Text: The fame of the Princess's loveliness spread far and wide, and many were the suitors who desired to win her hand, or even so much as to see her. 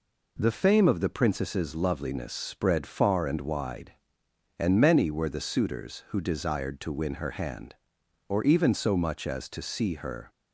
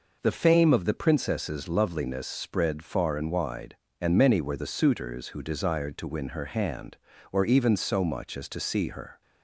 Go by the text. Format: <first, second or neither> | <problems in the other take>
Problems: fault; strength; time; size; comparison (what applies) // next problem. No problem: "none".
neither | none